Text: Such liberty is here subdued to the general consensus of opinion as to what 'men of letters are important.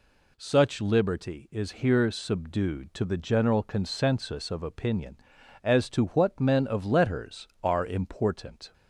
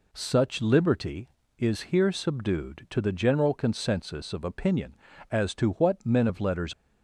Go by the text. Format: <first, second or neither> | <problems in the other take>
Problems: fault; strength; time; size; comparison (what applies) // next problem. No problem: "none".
first | stops before "are important"; at 6.7 s